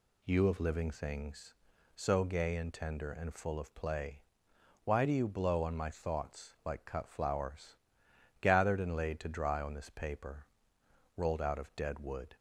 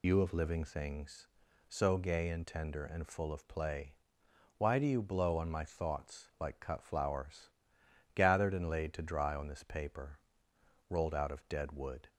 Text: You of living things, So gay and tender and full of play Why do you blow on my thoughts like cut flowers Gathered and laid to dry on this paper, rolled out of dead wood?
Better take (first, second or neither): first